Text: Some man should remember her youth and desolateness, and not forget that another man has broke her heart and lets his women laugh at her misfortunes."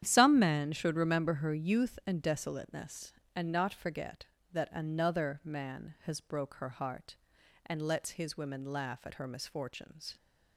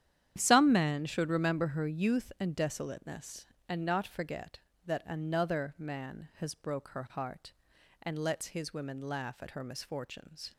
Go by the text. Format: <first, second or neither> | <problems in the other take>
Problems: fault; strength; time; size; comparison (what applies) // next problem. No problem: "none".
neither | starts louder than the rest; strong; the same in both